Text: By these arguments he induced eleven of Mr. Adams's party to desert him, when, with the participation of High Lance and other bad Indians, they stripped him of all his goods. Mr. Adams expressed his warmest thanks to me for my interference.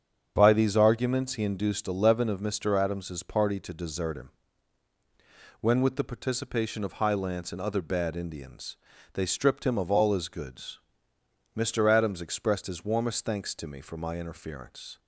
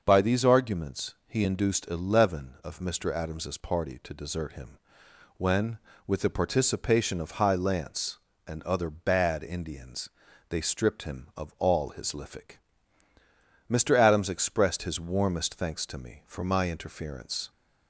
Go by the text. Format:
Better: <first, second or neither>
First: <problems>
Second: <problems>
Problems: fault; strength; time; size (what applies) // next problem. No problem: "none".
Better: first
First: starts louder than the rest; strong; until 1.3 s; 7 dB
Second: starts louder than the rest; until 1.0 s; 6 dB // says "lific" for "goods"; at 12.1 s